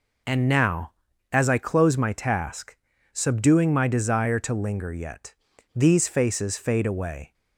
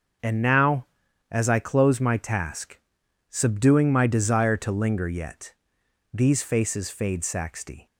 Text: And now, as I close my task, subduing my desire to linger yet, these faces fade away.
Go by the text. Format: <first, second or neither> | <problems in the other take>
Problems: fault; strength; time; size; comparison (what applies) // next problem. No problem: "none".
first | starts louder than the rest; until 1.6 s; 6.5 dB // says "saxty" for "away"; at 7.2 s